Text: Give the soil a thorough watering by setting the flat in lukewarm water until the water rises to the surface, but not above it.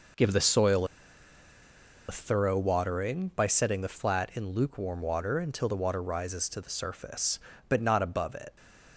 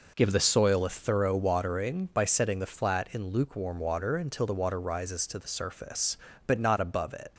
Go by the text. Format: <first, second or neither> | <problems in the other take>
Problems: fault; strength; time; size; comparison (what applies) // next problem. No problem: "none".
second | pauses between "soil" and "a"; at 0.8 s; 1.2 s long